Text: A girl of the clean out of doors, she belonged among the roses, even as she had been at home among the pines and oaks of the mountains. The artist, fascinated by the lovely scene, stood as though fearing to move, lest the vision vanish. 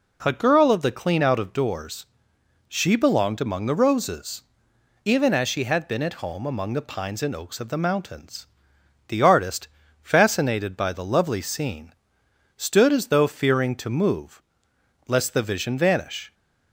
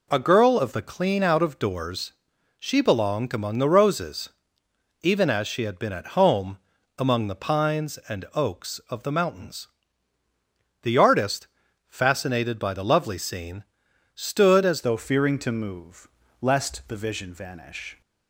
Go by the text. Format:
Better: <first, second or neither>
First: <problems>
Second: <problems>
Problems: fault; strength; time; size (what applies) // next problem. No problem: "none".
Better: first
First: none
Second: pauses between "home" and "among"; at 6.5 s; 0.40 s long // changes voice at "though"; from 14.8 s on; 3.2 s long